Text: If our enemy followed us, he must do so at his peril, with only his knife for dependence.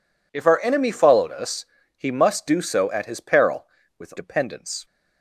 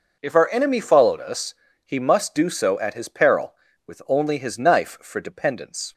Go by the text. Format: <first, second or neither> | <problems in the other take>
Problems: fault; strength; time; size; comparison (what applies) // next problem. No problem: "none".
second | skips "only his knife for"; at 4.1 s